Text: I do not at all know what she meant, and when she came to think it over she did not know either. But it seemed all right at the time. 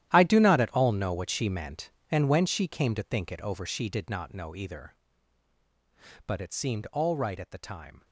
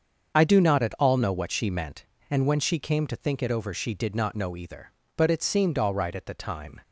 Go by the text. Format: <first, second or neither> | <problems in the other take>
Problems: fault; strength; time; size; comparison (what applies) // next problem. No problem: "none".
second | gets quieter; strong; throughout; 14.5 dB // starts louder than the rest; strong; until 1.1 s; 12 dB; also in the second